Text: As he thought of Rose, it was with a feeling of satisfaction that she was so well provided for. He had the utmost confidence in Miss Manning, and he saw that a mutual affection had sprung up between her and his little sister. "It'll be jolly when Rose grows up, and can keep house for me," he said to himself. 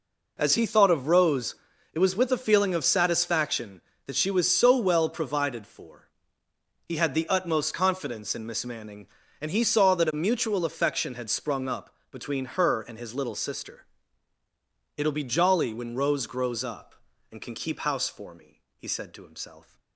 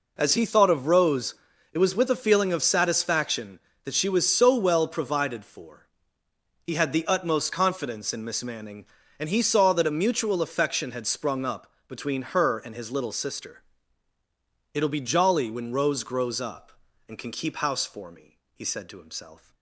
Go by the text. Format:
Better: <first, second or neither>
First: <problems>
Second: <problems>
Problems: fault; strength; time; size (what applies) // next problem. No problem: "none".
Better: neither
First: pauses between "up" and "between"; slight; at 11.9 s; 0.16 s long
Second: pauses between "up" and "between"; slight; at 11.7 s; 0.16 s long